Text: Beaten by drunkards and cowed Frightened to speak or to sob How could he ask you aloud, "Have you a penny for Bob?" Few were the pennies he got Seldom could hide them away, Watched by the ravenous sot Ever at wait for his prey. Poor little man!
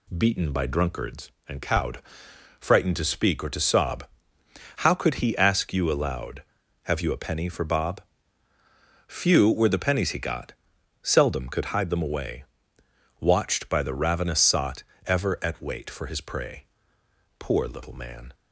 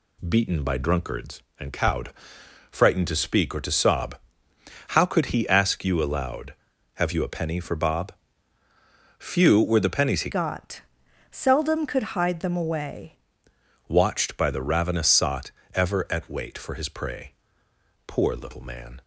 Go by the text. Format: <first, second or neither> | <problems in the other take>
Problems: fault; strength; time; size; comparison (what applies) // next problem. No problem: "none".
first | pauses between "cowed" and "Frightened"; noticeable; at 2.1 s; 0.60 s long; noticeable in the first // pauses between "sob" and "How"; noticeable; at 4.1 s; 0.72 s long; noticeable in the first // changes voice from "got" to "away"; from 10.3 to 13.1 s; 2.8 s long // pauses between "got" and "Seldom"; noticeable; at 10.8 s; 0.50 s long; noticeable in the first // pauses between "sot" and "Ever"; slight; at 15.5 s; 0.24 s long; slight in the first